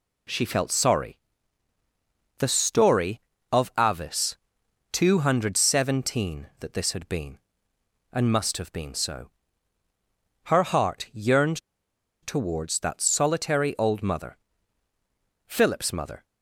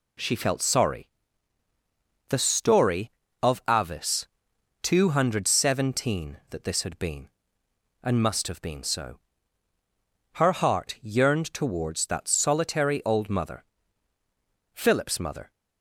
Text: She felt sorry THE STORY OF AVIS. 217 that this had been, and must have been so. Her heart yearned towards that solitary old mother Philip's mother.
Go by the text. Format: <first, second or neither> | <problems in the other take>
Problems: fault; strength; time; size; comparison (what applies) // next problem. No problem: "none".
second | pauses between "sorry" and "THE"; at 1.1 s; 1.2 s long; also in the second // pauses between "yearned" and "towards"; noticeable; at 11.5 s; 0.64 s long // pauses between "mother" and "Philip's"; at 14.3 s; 1.1 s long; also in the second